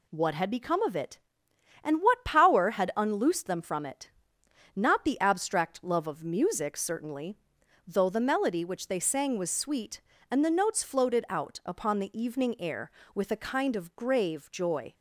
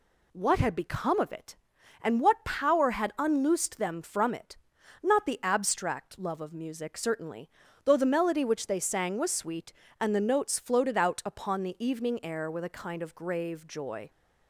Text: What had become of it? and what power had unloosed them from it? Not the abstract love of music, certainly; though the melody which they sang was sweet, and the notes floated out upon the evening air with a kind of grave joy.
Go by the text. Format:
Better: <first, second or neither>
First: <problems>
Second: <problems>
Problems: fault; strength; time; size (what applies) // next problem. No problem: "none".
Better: neither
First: none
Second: none